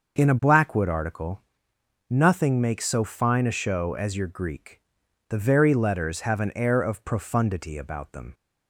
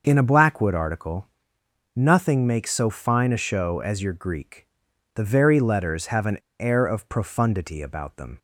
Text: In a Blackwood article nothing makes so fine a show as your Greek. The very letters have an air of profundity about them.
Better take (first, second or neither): first